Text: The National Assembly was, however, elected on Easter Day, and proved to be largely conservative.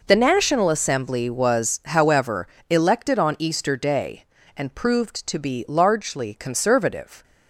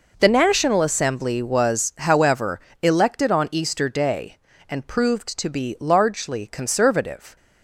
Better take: neither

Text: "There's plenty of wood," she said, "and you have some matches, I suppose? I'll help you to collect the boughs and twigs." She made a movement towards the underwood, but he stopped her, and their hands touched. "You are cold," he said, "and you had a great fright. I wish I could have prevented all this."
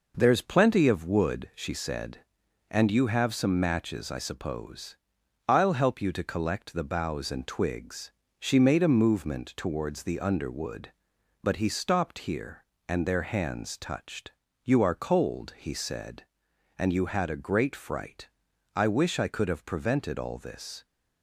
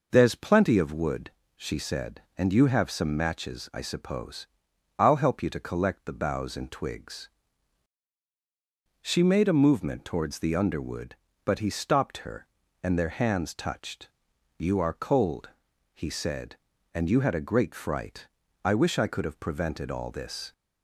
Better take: second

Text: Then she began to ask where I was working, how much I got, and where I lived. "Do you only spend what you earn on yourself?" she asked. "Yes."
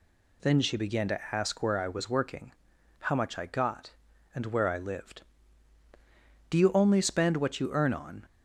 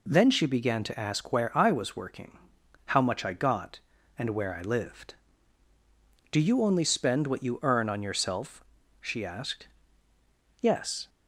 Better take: second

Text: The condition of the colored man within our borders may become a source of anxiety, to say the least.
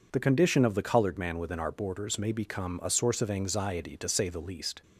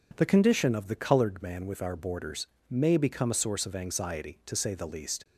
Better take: first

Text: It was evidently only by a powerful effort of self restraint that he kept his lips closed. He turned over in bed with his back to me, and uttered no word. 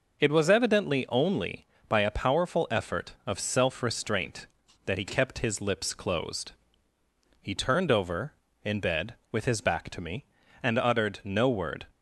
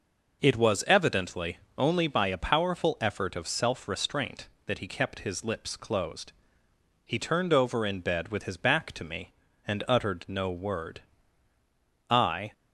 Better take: first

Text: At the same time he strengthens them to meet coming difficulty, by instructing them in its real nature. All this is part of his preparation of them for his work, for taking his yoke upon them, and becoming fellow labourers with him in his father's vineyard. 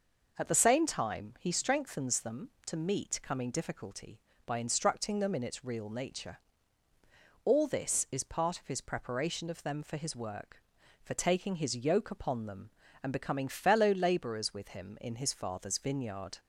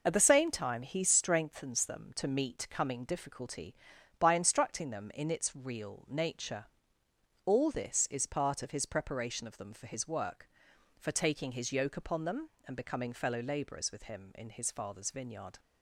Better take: first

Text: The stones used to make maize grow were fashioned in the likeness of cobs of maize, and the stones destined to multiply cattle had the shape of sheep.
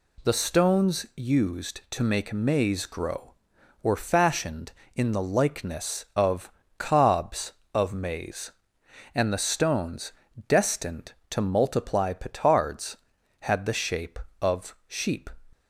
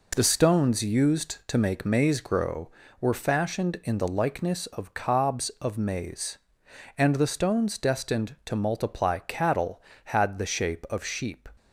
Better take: second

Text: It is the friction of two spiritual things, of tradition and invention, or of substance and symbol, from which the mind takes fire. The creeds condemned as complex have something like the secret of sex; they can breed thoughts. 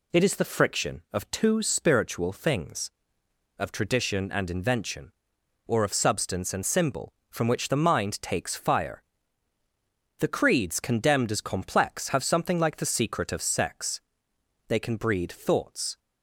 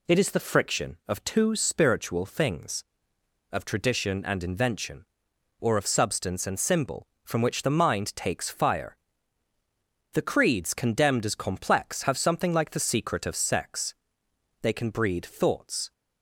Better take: neither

